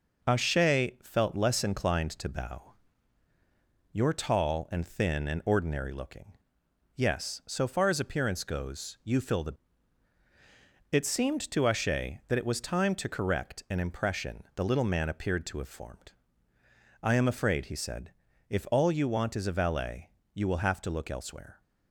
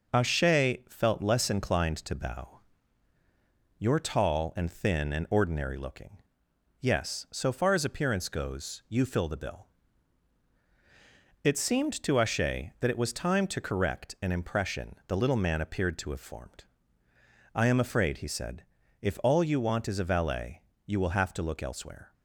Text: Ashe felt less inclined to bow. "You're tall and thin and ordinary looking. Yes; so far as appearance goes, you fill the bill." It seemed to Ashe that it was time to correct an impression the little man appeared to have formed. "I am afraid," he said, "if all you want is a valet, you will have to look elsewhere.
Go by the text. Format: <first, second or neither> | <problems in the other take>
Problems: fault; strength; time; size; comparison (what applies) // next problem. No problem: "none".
second | skips "bill"; at 10.2 s